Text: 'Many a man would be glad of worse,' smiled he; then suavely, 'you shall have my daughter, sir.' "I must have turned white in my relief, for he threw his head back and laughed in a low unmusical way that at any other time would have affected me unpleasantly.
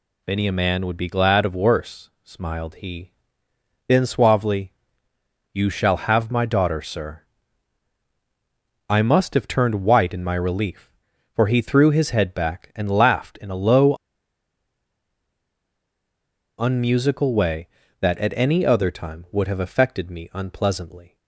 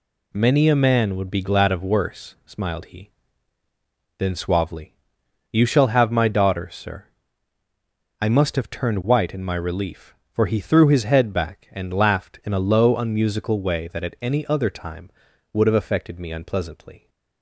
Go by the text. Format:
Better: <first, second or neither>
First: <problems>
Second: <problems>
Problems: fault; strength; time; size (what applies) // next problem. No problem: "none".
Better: second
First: pauses between "low" and "unmusical"; strong; at 13.9 s; 2.6 s long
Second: none